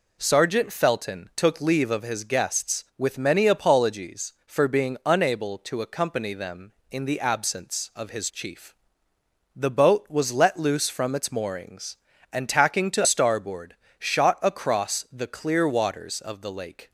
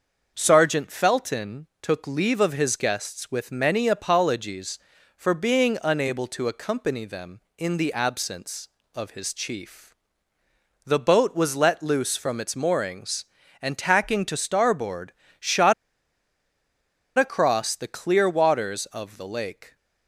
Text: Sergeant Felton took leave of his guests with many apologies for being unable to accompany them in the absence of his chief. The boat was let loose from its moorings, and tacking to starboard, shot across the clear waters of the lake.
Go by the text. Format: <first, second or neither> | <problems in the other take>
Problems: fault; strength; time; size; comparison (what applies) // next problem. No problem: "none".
first | starts louder than the rest; until 1.3 s; 6 dB // pauses between "shot" and "across"; strong; at 15.7 s; 1.4 s long